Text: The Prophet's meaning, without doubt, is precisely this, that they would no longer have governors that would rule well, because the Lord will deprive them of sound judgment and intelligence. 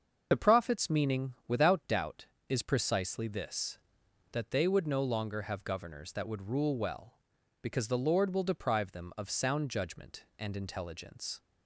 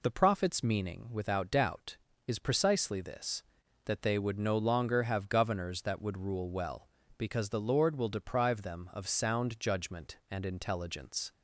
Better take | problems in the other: second | loses the start of "The"; at 0.3 s; 35 ms // starts louder than the rest; until 1.3 s; 6.5 dB

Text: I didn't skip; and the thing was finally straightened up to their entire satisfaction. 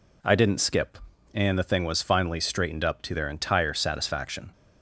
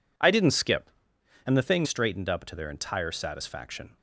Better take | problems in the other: first | skips "was finally"; at 1.8 s

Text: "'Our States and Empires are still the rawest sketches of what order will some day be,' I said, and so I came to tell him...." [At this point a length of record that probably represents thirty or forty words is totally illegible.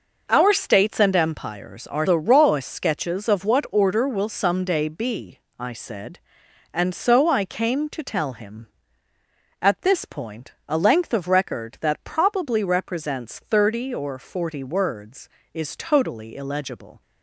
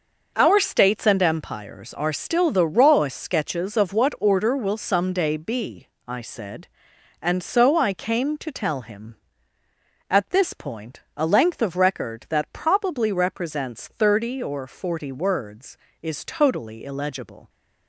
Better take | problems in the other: second | skips "still"; at 2.0 s // pauses between "point" and "a"; slight; at 10.5 s; 0.16 s long; slight in the second

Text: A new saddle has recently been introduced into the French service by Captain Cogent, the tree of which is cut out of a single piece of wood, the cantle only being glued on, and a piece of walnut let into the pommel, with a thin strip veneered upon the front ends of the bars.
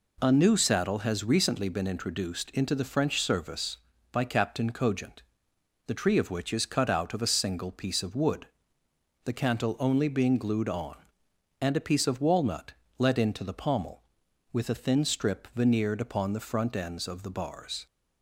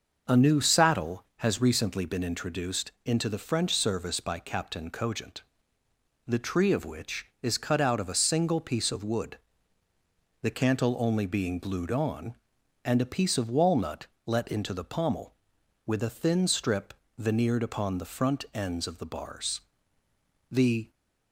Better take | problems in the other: first | starts louder than the rest; noticeable; until 1.4 s; 6 dB // pauses between "walnut" and "let"; slight; at 14.0 s; 0.18 s long; slight in the first // pauses between "strip" and "veneered"; slight; at 16.9 s; 0.24 s long // goes on to say "The"; slight; from 20.4 s on; 0.44 s long

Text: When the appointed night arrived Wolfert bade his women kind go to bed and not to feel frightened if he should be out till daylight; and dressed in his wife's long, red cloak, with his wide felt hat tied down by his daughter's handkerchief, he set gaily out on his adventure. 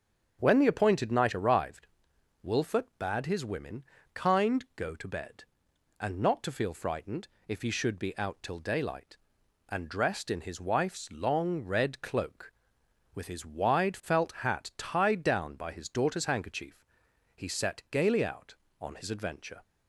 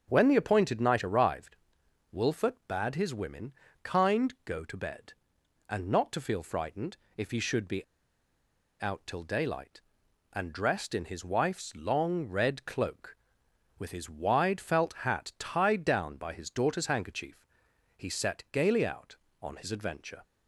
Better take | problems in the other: first | starts louder than the rest; until 1.0 s; 7 dB; also in the first // pauses between "arrived" and "Wolfert"; noticeable; at 1.5 s; 0.56 s long; noticeable in the first // pauses between "women" and "kind"; slight; at 3.5 s; 0.30 s long; slight in the first // pauses between "frightened" and "if"; slight; at 6.9 s; 0.18 s long; slight in the first // pauses between "be" and "out"; noticeable; at 7.8 s; 0.95 s long

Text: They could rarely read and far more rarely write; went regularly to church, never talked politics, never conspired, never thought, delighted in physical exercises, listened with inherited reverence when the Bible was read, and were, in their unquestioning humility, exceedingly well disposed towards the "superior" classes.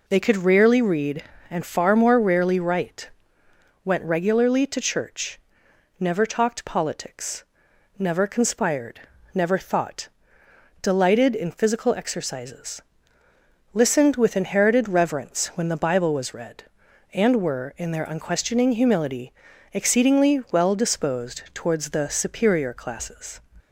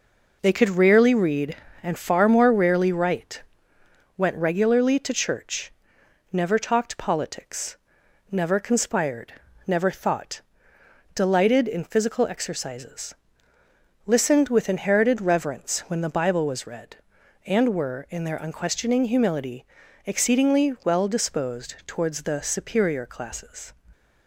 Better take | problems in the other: first | gets quieter; noticeable; throughout; 6 dB

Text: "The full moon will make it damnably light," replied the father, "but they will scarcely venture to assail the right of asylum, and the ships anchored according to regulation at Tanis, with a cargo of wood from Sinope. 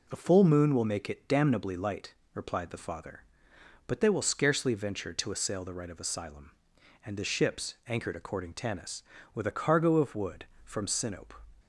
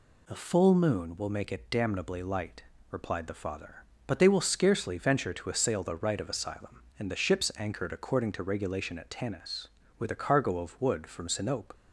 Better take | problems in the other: second | skips "to regulation at"; at 8.5 s

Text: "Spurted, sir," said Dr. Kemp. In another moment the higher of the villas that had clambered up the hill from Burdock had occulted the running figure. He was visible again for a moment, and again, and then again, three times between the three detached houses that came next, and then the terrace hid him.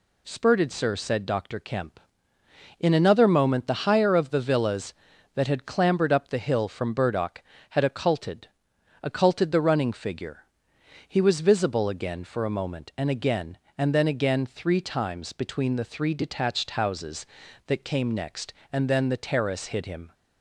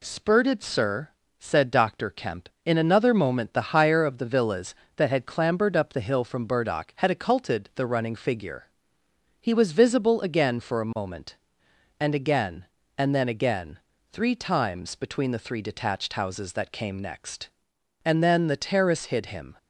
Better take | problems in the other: second | says "occulted" twice; at 9.0 s

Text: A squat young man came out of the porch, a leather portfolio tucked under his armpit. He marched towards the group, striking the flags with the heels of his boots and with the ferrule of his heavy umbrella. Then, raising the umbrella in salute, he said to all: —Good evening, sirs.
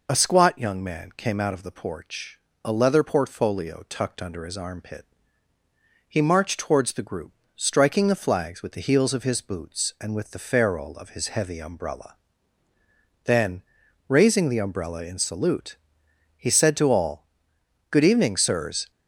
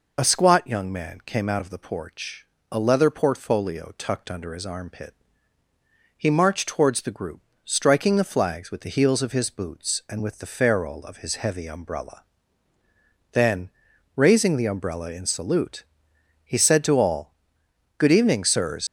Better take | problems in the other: first | leaves "sirs" unfinished; at 18.8 s; 105 ms

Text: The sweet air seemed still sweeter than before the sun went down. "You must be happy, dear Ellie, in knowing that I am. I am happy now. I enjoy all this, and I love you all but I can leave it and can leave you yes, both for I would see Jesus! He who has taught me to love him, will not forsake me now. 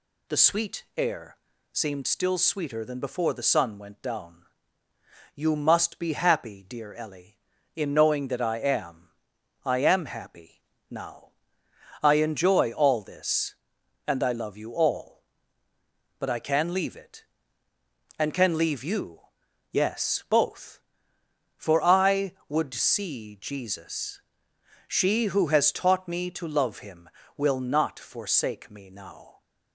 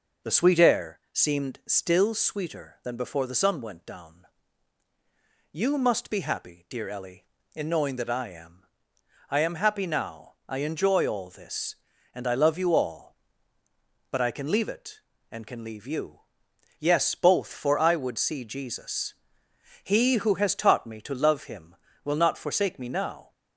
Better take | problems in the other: second | pauses between "air" and "seemed"; slight; at 1.3 s; 0.34 s long // pauses between "happy" and "now"; slight; at 10.6 s; 0.26 s long // pauses between "you" and "yes"; noticeable; at 19.2 s; 0.50 s long; noticeable in the second // says "She" for "He"; at 24.8 s

